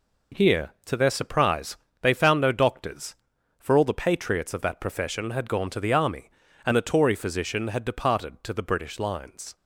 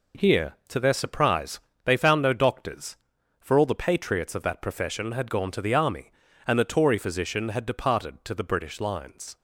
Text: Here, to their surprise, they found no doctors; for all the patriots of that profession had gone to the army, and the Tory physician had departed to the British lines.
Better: neither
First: none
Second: none

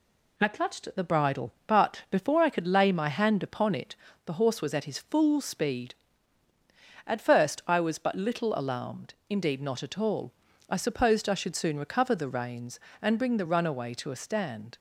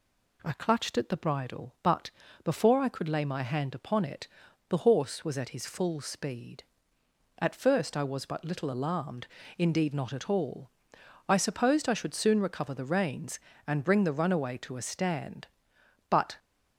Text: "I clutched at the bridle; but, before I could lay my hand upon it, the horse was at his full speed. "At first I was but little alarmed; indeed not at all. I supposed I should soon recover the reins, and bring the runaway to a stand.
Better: first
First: none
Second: goes on to say "But"; slight; from 16.0 s on; 0.28 s long

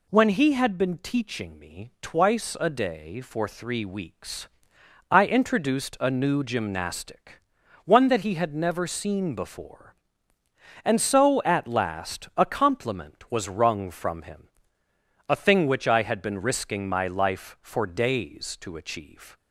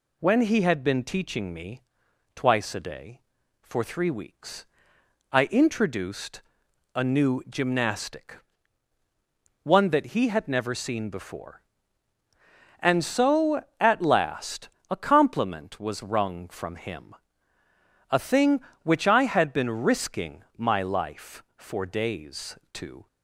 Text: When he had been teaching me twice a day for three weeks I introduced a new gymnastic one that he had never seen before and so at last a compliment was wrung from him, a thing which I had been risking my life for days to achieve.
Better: first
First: pauses between "weeks" and "I"; noticeable; at 4.4 s; 0.62 s long // pauses between "gymnastic" and "one"; at 7.4 s; 0.42 s long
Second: pauses between "me" and "twice"; noticeable; at 1.7 s; 0.56 s long // pauses between "weeks" and "I"; noticeable; at 4.6 s; 0.66 s long // pauses between "introduced" and "a"; noticeable; at 6.4 s; 0.52 s long // pauses between "gymnastic" and "one"; strong; at 8.3 s; 1.2 s long // pauses between "last" and "a"; slight; at 14.6 s; 0.22 s long // pauses between "risking" and "my"; slight; at 20.4 s; 0.16 s long // stops before "achieve"; at 23.0 s

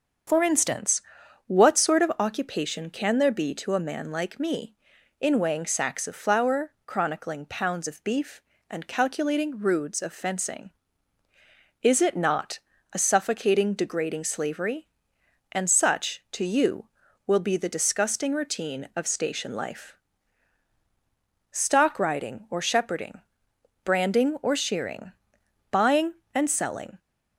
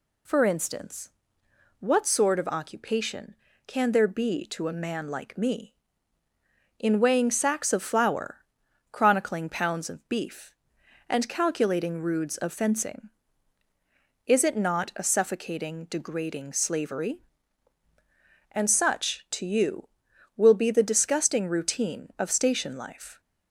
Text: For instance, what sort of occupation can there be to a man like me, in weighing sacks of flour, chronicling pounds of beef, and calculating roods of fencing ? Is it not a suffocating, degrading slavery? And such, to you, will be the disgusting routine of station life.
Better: second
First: starts louder than the rest; until 1.7 s; 6.5 dB // pauses between "not" and "a"; slight; at 12.5 s; 0.34 s long // goes on to say "Stock riding or shepherding branding or shearing buying and selling"; strong; from 21.5 s on; 5.4 s long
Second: none

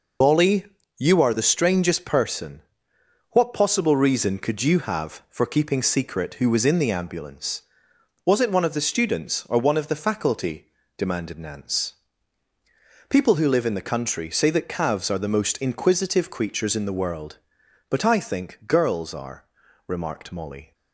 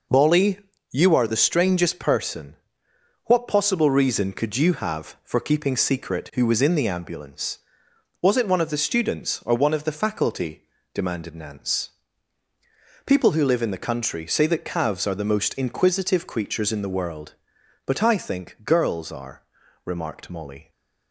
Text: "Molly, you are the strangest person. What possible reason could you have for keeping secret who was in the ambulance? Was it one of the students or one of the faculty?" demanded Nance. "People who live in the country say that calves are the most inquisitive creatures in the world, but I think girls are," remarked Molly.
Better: second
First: loses the start of "Molly"; at 0.2 s; 30 ms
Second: none

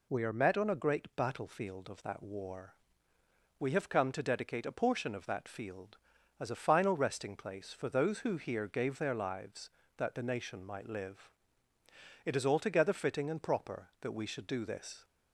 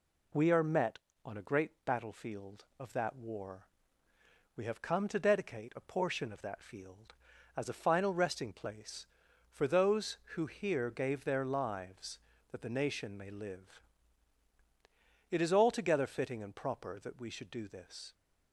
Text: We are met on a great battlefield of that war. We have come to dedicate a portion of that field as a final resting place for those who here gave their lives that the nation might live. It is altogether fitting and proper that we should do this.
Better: first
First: none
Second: says "may" for "might"; at 13.1 s

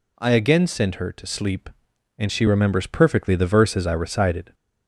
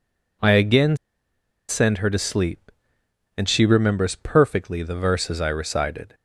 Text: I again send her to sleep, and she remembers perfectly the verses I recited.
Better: first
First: none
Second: pauses between "again" and "send"; noticeable; at 0.9 s; 0.73 s long

